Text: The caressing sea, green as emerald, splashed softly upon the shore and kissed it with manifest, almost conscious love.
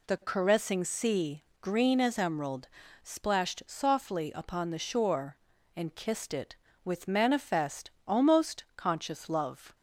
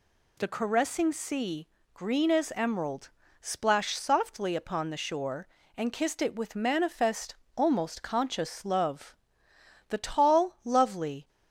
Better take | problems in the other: first | goes on to say "The tall lovely"; from 9.8 s on; 1.4 s long

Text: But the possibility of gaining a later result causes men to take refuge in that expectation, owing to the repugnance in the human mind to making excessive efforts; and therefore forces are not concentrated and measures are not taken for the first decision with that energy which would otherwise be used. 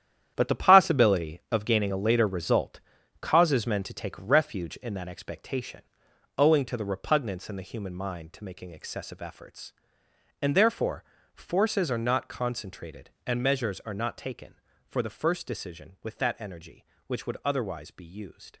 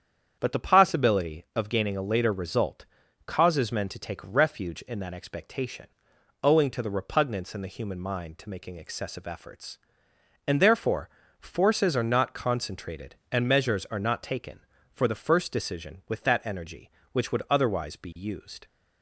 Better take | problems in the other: second | gets quieter; strong; throughout; 11 dB // starts louder than the rest; strong; until 1.3 s; 10 dB; strong in the second // pauses between "result" and "causes"; at 2.7 s; 0.42 s long; also in the second // pauses between "therefore" and "forces"; slight; at 11.0 s; 0.32 s long; slight in the second

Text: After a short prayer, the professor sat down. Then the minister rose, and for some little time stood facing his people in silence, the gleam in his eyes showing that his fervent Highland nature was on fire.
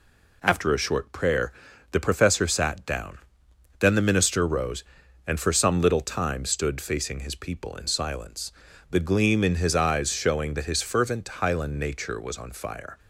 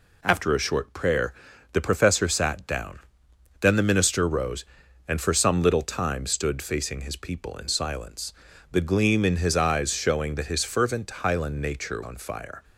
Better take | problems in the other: first | skips "was"; at 12.0 s

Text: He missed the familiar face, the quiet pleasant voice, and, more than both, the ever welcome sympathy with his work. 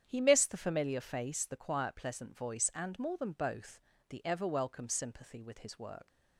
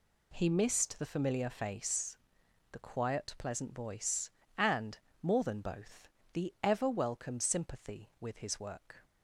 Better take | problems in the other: second | starts louder than the rest; strong; until 1.0 s; 9 dB // leaves "work" unfinished; at 6.0 s; 100 ms

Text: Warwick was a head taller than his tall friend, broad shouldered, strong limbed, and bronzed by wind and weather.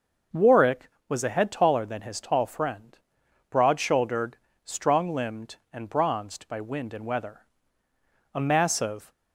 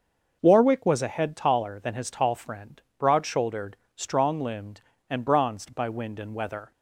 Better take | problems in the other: second | starts louder than the rest; noticeable; until 1.5 s; 6 dB; also in the second // goes on to say "A massive"; noticeable; from 8.3 s on; 0.78 s long

